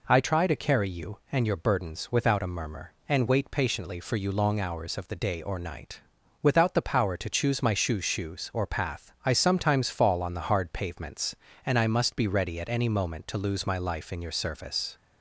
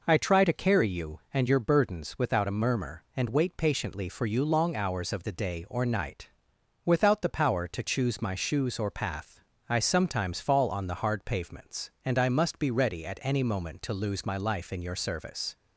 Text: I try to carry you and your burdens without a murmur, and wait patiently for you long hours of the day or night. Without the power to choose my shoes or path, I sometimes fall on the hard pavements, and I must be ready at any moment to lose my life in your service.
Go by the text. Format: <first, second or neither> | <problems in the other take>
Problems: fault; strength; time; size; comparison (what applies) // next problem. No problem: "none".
second | says "shoes" twice; at 8.0 s